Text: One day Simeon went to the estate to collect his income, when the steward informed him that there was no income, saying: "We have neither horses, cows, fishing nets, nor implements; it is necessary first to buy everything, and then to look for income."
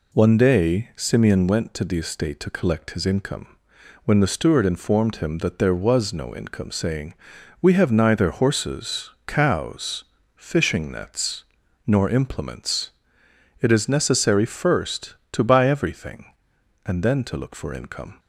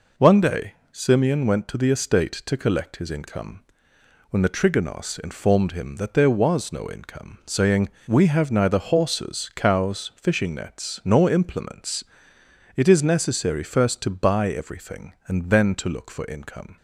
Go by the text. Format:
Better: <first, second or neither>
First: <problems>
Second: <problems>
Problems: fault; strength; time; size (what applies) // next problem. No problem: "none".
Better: first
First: none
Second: pauses between "day" and "Simeon"; slight; at 0.7 s; 0.20 s long // says "trigonos" for "steward"; at 4.4 s